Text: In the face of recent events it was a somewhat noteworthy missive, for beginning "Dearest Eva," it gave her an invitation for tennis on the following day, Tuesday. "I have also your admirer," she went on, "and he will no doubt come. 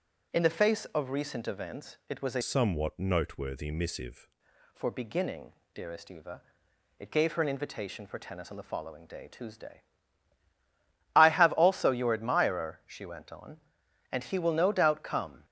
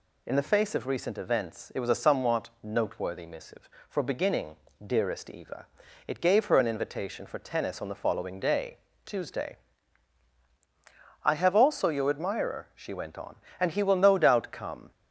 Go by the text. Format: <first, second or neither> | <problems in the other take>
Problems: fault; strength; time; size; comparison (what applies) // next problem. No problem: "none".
second | starts louder than the rest; strong; until 1.4 s; 7 dB // changes voice from "somewhat" to "missive"; from 2.4 to 4.2 s; 1.8 s long // pauses between "beginning" and "Dearest"; slight; at 5.5 s; 0.20 s long; slight in the second